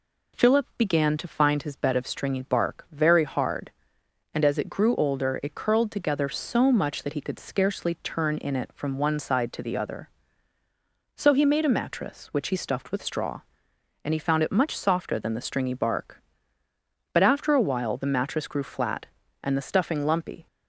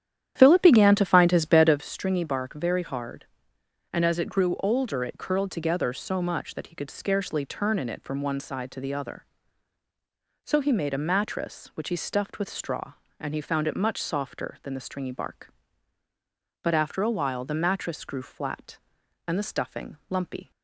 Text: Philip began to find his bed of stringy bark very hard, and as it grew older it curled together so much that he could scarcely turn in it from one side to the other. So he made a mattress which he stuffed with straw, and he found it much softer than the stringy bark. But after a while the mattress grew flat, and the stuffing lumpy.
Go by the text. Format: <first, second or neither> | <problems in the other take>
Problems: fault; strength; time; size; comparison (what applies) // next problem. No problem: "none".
first | starts louder than the rest; strong; until 1.9 s; 10.5 dB